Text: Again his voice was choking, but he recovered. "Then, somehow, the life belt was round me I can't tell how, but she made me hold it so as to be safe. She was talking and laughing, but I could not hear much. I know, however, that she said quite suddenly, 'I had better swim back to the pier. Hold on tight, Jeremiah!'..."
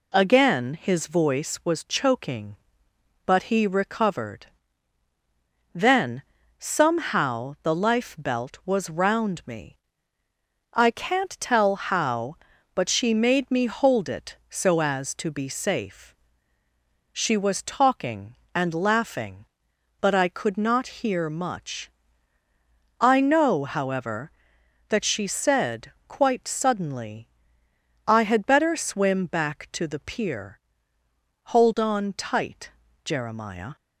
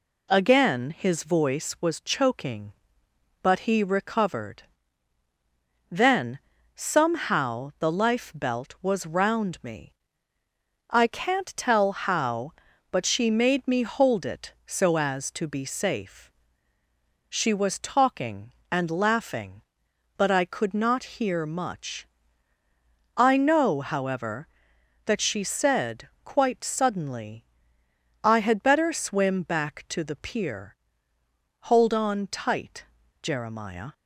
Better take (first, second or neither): neither